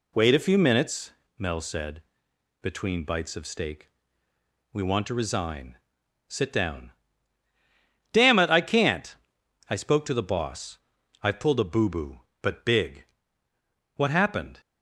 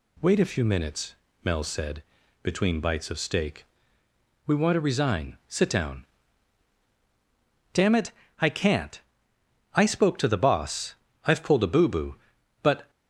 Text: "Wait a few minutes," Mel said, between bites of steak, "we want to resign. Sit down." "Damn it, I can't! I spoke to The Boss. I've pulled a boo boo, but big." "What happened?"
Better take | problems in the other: first | stops before "big What happened"; at 12.8 s

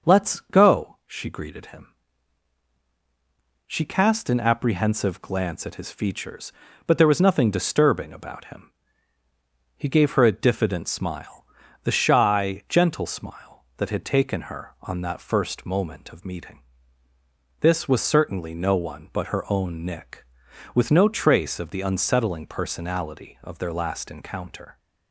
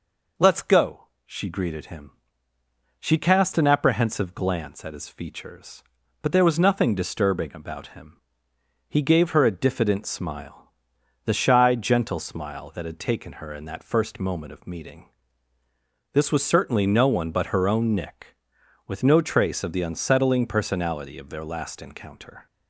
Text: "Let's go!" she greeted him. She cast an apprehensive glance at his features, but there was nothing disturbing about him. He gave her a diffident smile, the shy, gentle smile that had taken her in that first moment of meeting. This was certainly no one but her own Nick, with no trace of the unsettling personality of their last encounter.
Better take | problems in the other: second | starts louder than the rest; noticeable; until 1.1 s; 6 dB // says "on" for "in"; at 14.8 s

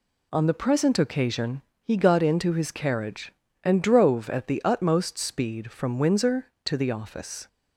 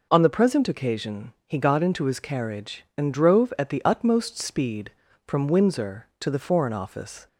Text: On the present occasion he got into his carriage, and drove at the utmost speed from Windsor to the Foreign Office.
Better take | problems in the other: second | pauses between "occasion" and "he"; slight; at 1.6 s; 0.20 s long; slight in the second // skips "Foreign"; at 6.9 s

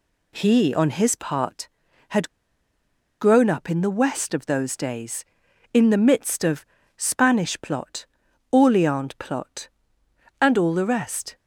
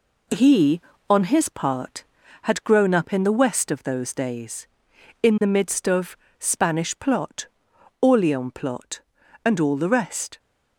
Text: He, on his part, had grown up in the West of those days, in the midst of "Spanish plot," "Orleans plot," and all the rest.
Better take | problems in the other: second | pauses between "had" and "grown"; noticeable; at 2.2 s; 0.91 s long // pauses between "of" and "Spanish"; slight; at 6.6 s; 0.32 s long; slight in the second

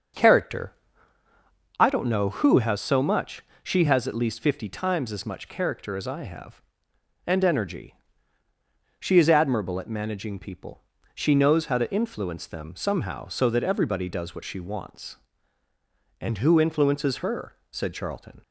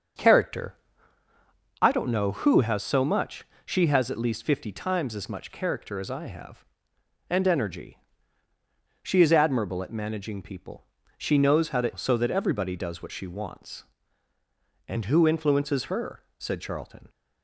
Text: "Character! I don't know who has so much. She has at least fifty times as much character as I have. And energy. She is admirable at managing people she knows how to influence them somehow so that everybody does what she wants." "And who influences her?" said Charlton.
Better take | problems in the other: first | starts louder than the rest; until 2.2 s; 7 dB; also in the first // pauses between "people" and "she"; slight; at 10.8 s; 0.36 s long; slight in the first // skips "influence them somehow"; at 11.9 s

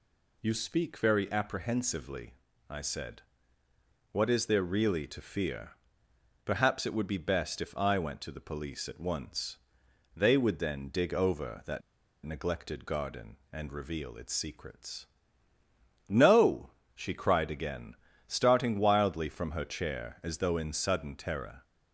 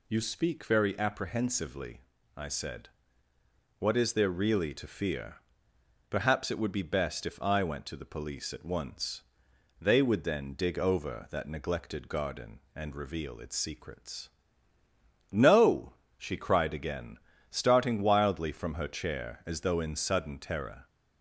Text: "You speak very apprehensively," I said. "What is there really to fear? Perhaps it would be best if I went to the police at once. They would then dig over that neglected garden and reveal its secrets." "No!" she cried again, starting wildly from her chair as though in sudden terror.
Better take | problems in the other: second | pauses between "that" and "neglected"; at 11.8 s; 0.44 s long

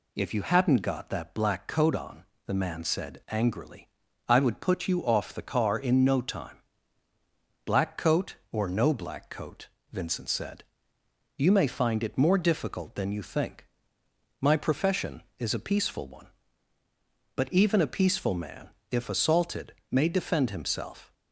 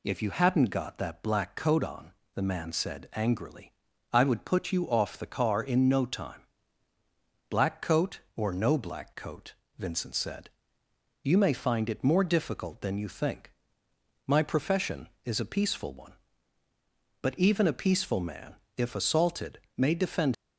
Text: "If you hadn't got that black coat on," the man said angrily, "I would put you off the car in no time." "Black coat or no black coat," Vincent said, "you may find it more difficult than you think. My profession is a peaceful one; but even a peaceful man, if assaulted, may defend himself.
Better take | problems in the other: first | stops before "himself"; at 20.3 s

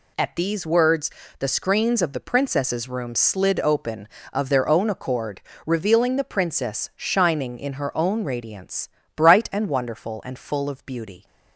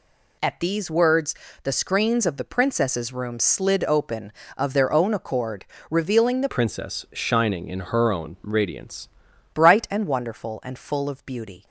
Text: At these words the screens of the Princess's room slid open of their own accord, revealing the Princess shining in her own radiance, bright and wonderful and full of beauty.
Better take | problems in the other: first | pauses between "words" and "the"; slight; at 1.3 s; 0.30 s long; slight in the first // changes voice from "Princess" to "radiance"; from 6.4 to 9.0 s; 2.6 s long

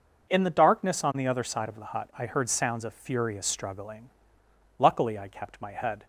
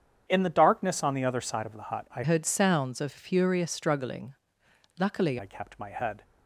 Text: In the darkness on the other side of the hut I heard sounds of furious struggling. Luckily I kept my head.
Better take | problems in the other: first | starts louder than the rest; strong; until 1.2 s; 8 dB // changes voice from "heard" to "Luckily"; from 2.2 to 5.3 s; 3.1 s long

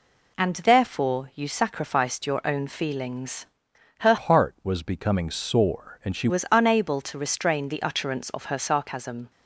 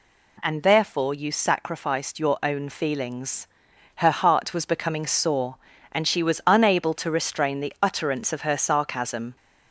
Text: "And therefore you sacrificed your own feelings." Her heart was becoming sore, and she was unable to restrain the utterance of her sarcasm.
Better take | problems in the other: second | changes voice from "heart" to "she"; from 4.1 to 6.2 s; 2.1 s long

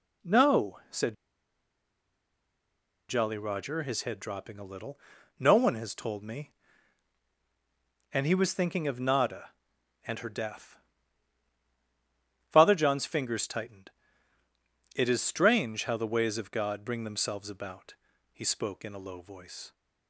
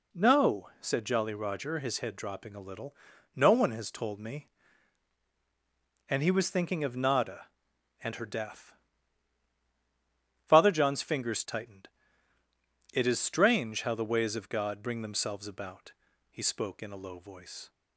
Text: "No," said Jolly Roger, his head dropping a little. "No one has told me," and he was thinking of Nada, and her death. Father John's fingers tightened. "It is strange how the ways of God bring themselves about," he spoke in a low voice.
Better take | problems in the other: second | pauses between "said" and "Jolly"; strong; at 1.1 s; 1.9 s long

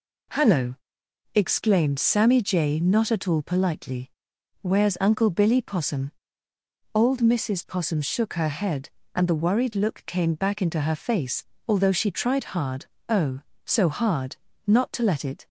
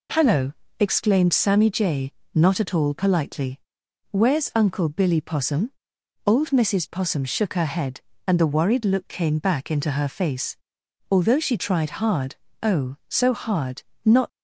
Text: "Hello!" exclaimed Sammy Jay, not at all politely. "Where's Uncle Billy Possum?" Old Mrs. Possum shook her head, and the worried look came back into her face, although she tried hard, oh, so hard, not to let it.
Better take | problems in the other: first | stops before "to let it"; at 14.2 s

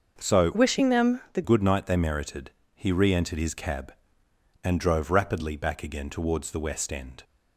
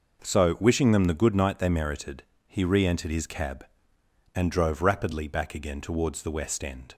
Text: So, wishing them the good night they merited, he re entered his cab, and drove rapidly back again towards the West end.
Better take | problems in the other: second | starts louder than the rest; until 1.1 s; 6 dB // changes voice from "wishing" to "the"; from 0.5 to 1.4 s; 0.9 s long

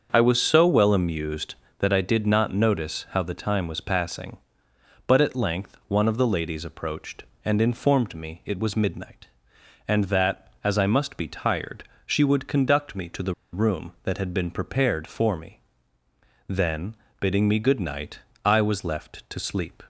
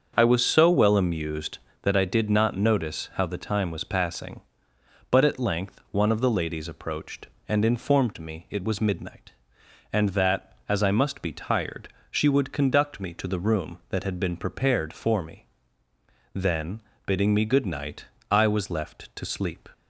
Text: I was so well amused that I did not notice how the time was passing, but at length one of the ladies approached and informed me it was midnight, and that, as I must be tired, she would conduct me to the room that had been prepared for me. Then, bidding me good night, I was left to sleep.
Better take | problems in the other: second | starts louder than the rest; until 1.1 s; 6.5 dB; also in the second // pauses between "the" and "room"; slight; at 13.3 s; 0.19 s long

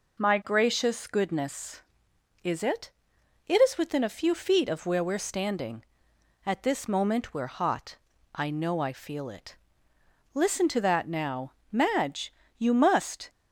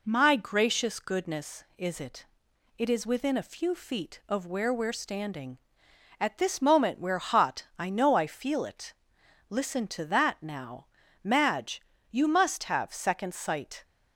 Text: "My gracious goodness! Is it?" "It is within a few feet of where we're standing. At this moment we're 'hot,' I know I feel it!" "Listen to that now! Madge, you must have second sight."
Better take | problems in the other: second | stops before "have second sight"; at 13.2 s

